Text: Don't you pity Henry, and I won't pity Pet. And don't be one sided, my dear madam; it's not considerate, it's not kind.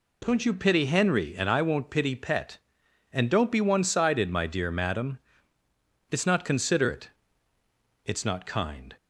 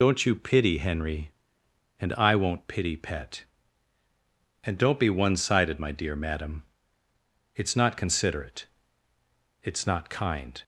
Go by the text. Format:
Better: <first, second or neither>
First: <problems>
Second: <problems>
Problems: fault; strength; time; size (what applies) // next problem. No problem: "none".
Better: first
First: none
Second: loses the start of "Don't"; at 0.0 s; 35 ms